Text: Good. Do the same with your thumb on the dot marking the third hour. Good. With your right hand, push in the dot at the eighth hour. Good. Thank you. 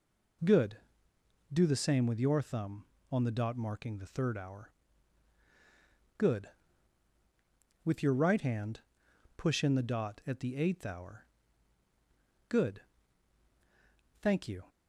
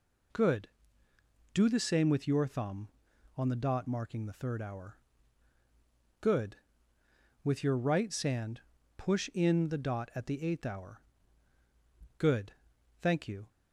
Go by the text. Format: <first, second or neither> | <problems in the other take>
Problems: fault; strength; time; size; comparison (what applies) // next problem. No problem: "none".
first | says "sand" for "hand"; at 8.1 s